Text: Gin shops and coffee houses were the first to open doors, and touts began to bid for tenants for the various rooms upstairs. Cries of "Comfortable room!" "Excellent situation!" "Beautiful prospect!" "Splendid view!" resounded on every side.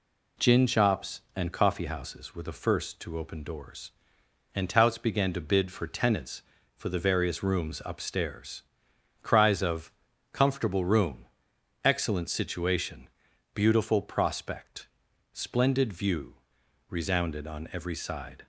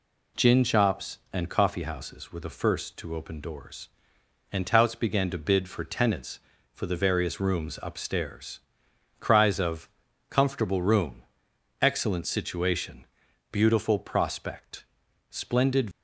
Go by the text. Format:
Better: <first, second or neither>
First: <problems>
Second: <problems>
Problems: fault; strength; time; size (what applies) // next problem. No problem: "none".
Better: first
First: pauses between "of" and "Comfortable"; at 9.9 s; 0.40 s long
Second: pauses between "of" and "Comfortable"; at 9.8 s; 0.40 s long // stops before "view resounded on every side"; at 15.9 s